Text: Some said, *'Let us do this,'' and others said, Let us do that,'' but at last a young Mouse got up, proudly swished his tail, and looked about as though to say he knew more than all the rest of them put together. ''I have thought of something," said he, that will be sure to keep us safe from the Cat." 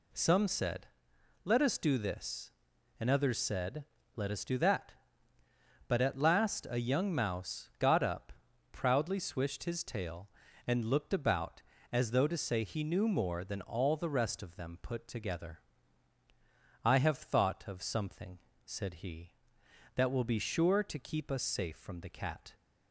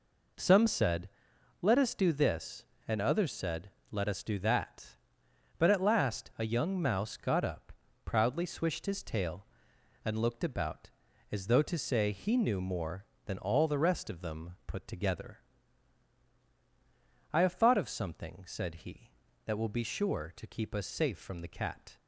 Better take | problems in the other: neither | none

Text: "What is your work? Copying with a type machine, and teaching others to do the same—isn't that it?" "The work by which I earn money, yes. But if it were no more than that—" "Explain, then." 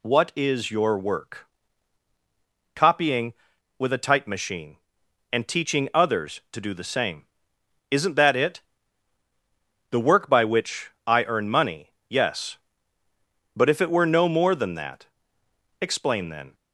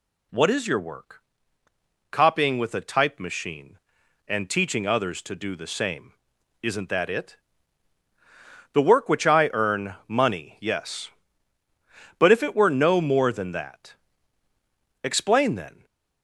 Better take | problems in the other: first | skips "by"; at 9.0 s // stays silent after the last word; slight; from 15.7 s on; 0.5 s long

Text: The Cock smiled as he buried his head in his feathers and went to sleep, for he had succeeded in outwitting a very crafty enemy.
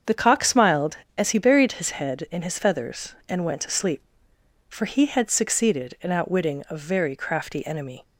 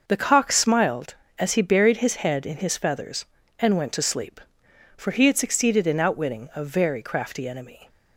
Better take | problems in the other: neither | starts louder than the rest; the same in both

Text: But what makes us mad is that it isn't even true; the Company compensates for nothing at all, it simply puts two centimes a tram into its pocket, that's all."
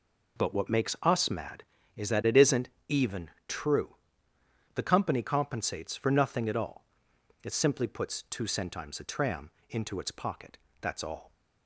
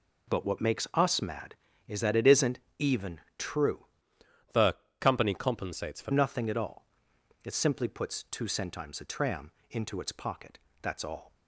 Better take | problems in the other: first | pauses between "isn't" and "even"; slight; at 2.5 s; 0.18 s long; slight in the first // pauses between "even" and "true"; slight; at 3.2 s; 0.18 s long; slight in the first // changes voice from "the" to "for"; from 4.5 to 6.1 s; 1.6 s long // pauses between "the" and "Company"; slight; at 4.7 s; 0.24 s long // pauses between "tram" and "into"; slight; at 9.5 s; 0.18 s long; slight in the first

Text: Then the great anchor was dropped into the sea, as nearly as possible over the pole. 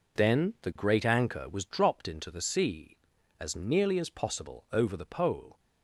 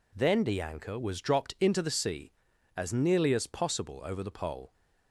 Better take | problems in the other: first | skips "great"; at 0.6 s

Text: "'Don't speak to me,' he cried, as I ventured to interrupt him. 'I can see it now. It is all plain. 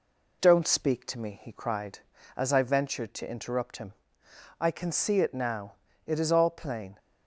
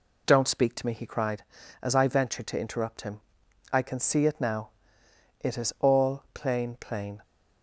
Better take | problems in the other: first | says "plain" twice; at 6.7 s

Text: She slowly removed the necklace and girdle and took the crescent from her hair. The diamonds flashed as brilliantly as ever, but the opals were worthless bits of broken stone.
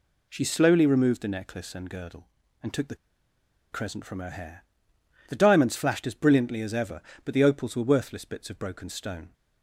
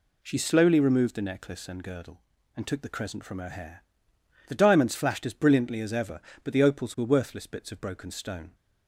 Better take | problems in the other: second | pauses between "the" and "crescent"; noticeable; at 2.9 s; 0.75 s long

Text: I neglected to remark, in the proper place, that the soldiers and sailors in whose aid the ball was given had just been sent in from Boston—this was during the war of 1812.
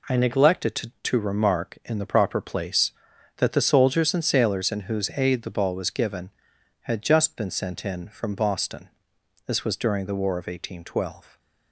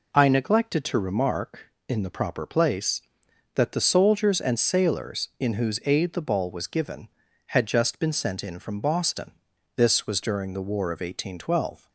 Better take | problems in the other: second | says "to" twice; at 1.0 s

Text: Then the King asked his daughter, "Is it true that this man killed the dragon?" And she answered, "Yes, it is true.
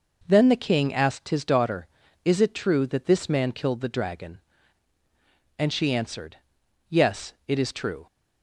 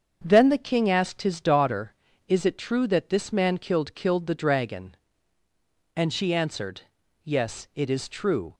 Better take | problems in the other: first | starts louder than the rest; until 1.2 s; 7 dB // says "killed" twice; at 3.9 s

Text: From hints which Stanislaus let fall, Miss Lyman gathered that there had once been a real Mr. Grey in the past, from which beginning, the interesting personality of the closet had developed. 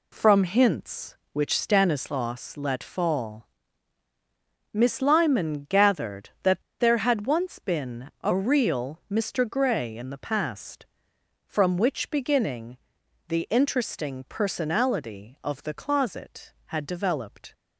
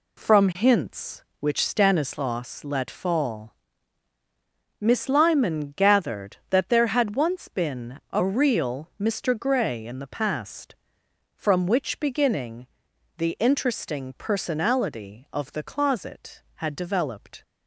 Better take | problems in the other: second | pauses between "that" and "there"; slight; at 6.6 s; 0.18 s long

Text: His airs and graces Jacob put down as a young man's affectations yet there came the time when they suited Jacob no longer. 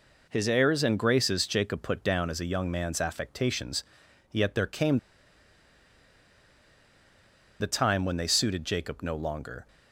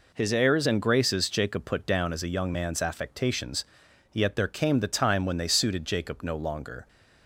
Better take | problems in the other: second | pauses between "affectations" and "yet"; noticeable; at 3.8 s; 0.48 s long; noticeable in the second // pauses between "came" and "the"; strong; at 4.9 s; 2.6 s long

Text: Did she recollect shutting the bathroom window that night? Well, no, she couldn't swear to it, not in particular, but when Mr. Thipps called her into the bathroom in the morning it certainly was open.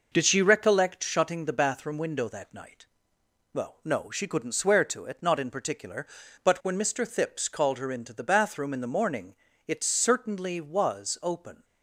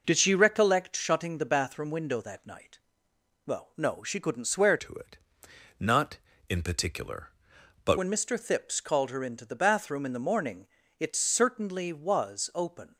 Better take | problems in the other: first | changes voice from "to" to "but"; from 4.7 to 7.9 s; 3.2 s long // pauses between "morning" and "it"; slight; at 10.6 s; 0.32 s long; slight in the first

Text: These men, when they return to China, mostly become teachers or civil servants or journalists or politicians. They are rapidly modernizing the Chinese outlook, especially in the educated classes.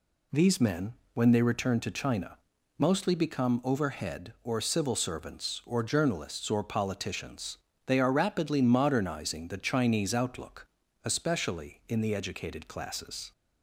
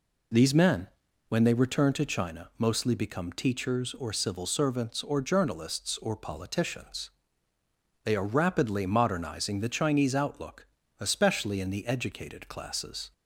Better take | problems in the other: second | says "overhead" for "teachers"; at 3.6 s

